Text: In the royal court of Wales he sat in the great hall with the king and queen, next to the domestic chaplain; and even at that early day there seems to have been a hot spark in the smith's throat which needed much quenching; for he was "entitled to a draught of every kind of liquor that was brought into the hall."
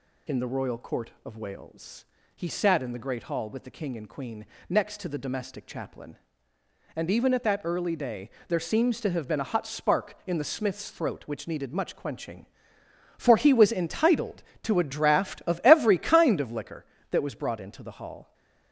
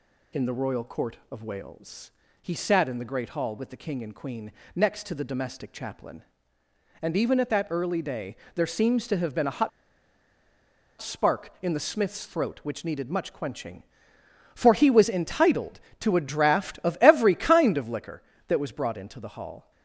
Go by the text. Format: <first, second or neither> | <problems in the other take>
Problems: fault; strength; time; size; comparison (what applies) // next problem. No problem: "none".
first | pauses between "Wales" and "he"; slight; at 2.0 s; 0.32 s long; slight in the first // pauses between "day" and "there"; slight; at 8.3 s; 0.20 s long; slight in the first // pauses between "hot" and "spark"; strong; at 9.6 s; 1.3 s long